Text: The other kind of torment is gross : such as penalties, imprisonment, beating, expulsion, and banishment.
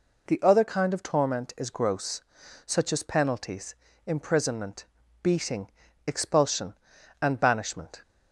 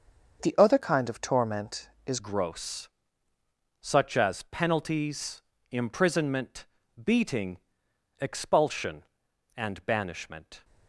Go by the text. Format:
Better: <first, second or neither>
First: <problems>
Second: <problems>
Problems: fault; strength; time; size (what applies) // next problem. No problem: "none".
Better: first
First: none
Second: starts louder than the rest; until 1.4 s; 6.5 dB // changes voice at "gross"; from 2.1 s on; 8.5 s long